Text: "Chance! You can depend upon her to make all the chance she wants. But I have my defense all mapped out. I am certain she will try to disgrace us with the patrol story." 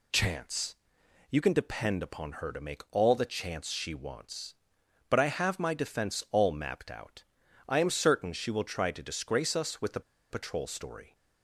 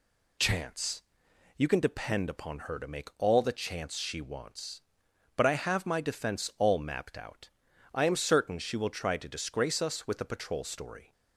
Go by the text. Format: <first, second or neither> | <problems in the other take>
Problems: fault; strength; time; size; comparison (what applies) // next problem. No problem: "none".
second | pauses between "the" and "patrol"; slight; at 10.0 s; 0.30 s long